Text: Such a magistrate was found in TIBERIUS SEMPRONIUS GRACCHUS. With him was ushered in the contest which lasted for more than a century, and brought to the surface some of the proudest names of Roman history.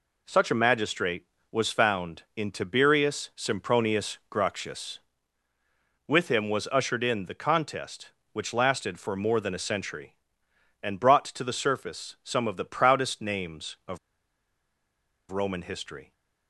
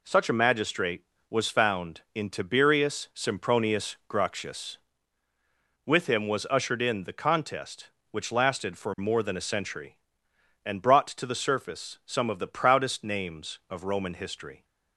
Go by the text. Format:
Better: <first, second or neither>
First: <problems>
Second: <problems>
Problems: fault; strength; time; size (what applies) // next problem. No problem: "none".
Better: second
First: pauses between "of" and "Roman"; strong; at 13.9 s; 1.3 s long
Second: none